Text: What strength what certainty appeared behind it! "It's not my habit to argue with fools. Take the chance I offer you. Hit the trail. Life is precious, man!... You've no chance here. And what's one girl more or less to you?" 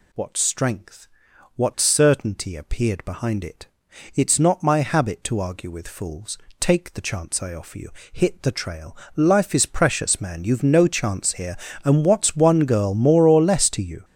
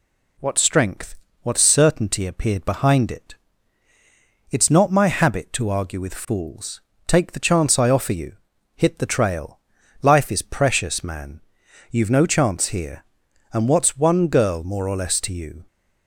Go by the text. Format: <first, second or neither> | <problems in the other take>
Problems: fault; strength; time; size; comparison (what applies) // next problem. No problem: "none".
second | gets louder; strong; throughout; 11 dB // pauses between "strength" and "what"; noticeable; at 1.0 s; 0.48 s long; slight in the second